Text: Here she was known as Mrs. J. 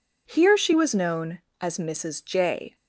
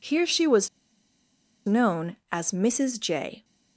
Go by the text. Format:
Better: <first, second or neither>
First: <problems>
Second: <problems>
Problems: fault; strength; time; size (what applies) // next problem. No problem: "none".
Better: first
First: none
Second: pauses between "was" and "known"; noticeable; at 0.6 s; 0.97 s long